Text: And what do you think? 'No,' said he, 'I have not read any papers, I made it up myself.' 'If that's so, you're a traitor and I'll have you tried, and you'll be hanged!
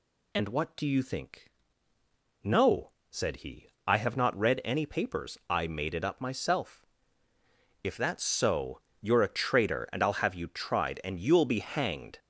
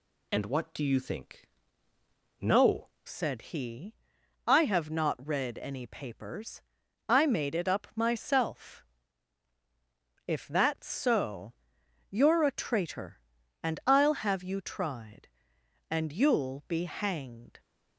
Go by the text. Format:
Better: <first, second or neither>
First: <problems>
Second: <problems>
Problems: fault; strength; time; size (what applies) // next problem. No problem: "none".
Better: first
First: none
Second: changes voice at "said"; from 3.0 s on; 14.5 s long